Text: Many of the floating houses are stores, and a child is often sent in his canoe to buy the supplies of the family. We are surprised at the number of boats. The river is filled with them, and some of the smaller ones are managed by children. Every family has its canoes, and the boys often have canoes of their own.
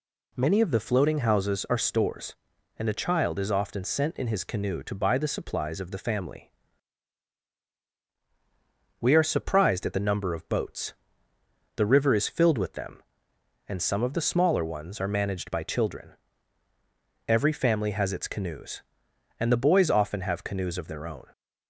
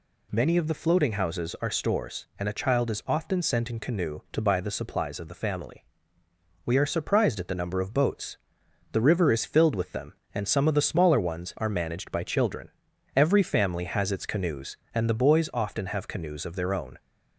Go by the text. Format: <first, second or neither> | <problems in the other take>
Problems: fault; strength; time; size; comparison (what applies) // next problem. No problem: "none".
first | skips "his"; at 3.7 s